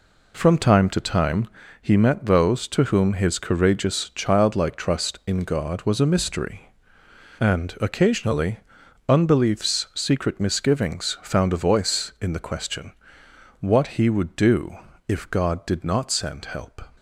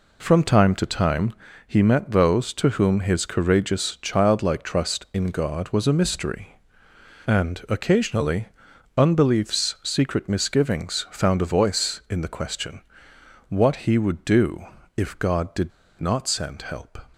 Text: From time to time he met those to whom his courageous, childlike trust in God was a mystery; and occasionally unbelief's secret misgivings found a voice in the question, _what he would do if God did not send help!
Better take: first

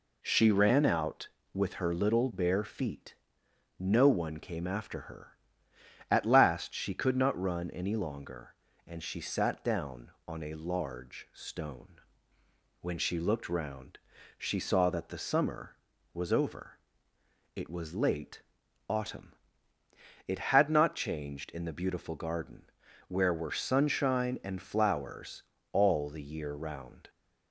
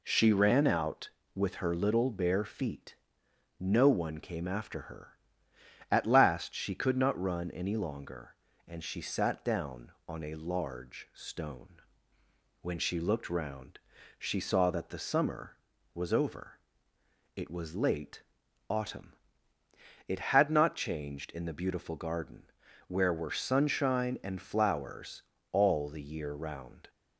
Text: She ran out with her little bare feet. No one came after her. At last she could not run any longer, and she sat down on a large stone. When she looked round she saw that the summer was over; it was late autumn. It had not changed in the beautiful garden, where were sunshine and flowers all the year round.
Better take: neither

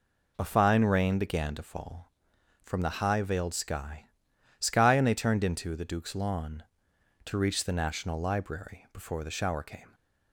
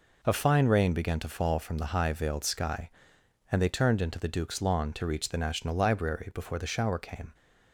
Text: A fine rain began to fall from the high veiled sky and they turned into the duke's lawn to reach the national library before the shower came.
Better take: second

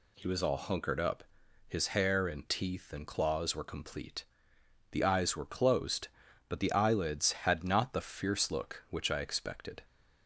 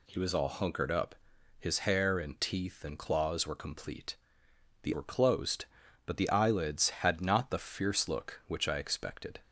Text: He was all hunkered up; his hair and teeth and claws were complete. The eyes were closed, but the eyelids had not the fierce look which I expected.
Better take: first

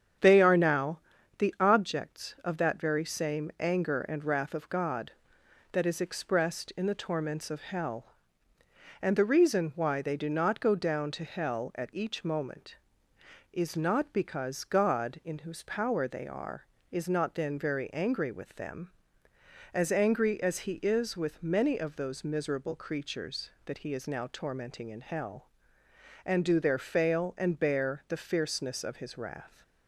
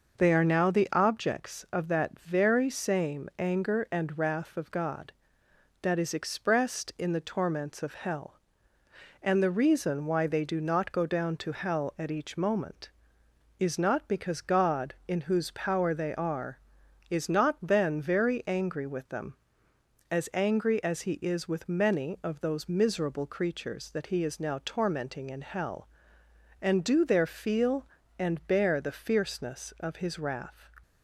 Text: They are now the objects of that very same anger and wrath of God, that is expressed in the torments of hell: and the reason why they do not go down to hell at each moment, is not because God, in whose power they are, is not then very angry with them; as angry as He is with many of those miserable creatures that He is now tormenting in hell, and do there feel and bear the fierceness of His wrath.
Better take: second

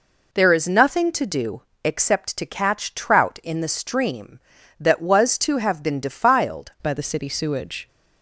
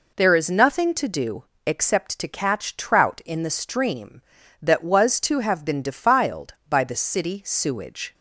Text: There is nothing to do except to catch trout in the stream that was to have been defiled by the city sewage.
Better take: second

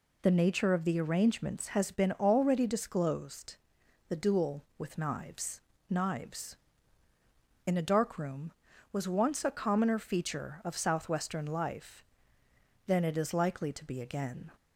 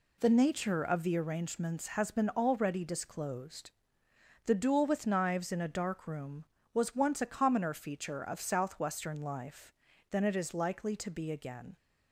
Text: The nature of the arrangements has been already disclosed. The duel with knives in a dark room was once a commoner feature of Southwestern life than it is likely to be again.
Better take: second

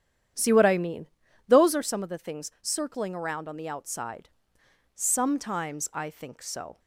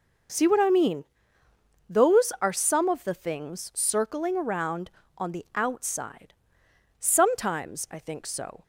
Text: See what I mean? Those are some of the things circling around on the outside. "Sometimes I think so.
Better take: second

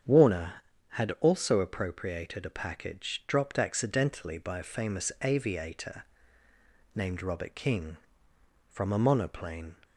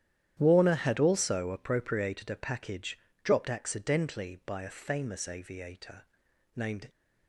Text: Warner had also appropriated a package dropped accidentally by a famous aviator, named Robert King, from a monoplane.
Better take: first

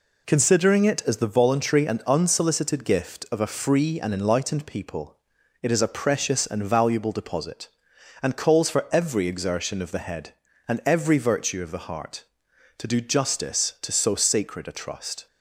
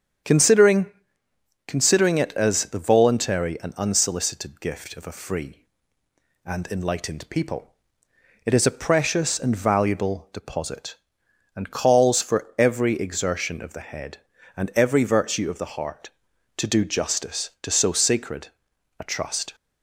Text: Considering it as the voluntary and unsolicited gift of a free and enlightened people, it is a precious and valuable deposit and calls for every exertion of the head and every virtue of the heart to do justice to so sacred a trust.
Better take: first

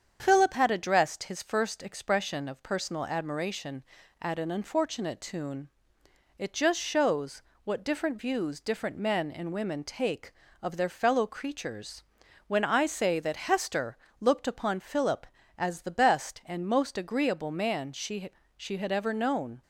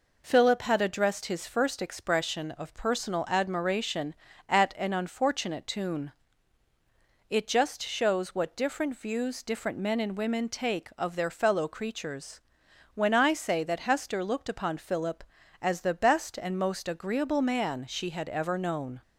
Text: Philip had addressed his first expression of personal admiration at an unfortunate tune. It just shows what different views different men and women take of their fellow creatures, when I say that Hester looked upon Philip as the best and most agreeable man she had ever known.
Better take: second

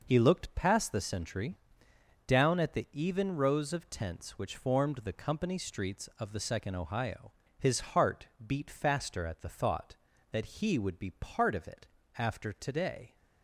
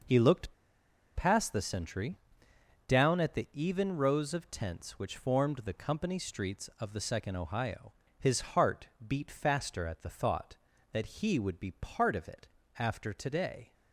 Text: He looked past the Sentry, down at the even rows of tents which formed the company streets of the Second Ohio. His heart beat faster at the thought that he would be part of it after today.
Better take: first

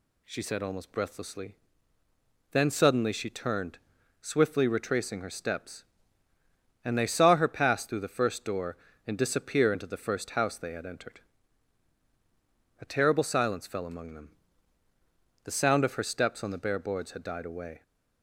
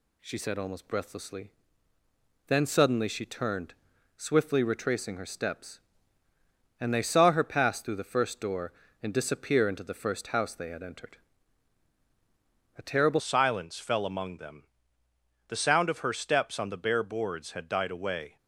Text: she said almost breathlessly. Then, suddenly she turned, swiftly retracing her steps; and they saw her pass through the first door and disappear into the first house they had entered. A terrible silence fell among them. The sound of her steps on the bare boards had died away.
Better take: first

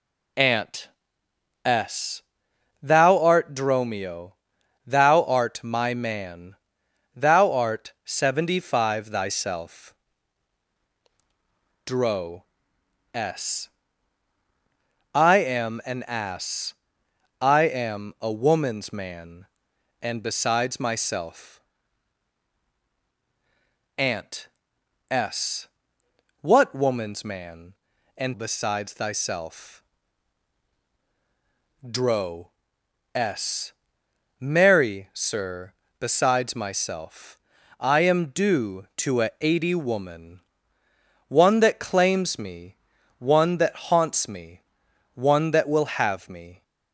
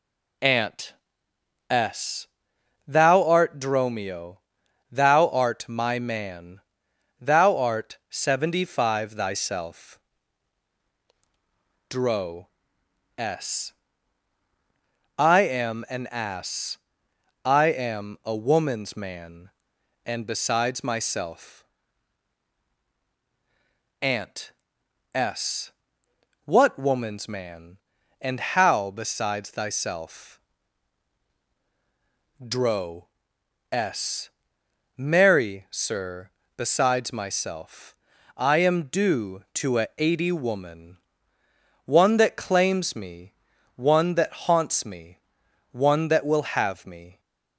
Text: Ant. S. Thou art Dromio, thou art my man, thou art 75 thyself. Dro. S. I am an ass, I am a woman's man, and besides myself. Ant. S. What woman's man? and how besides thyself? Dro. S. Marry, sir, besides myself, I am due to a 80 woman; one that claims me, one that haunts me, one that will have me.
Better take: second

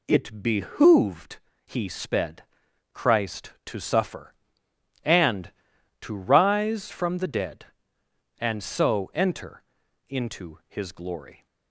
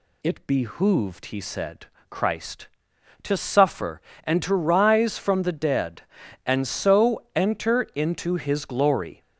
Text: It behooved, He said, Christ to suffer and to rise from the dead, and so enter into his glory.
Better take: second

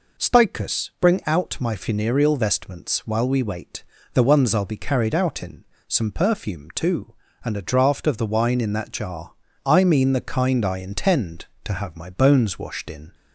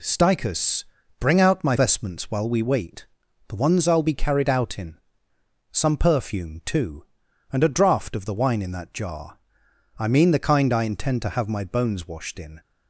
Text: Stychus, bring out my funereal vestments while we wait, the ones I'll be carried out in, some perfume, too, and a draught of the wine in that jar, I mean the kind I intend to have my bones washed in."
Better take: first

